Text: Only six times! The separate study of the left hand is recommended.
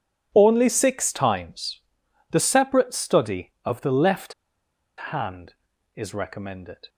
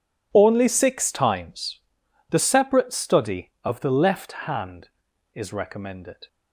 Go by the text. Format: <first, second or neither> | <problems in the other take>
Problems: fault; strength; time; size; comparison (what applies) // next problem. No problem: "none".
second | pauses between "left" and "hand"; noticeable; at 4.3 s; 0.77 s long